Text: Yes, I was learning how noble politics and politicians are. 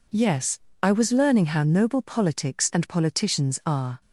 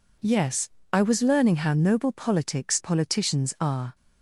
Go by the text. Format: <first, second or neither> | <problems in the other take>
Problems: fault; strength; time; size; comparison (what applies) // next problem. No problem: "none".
first | skips "and"; at 2.8 s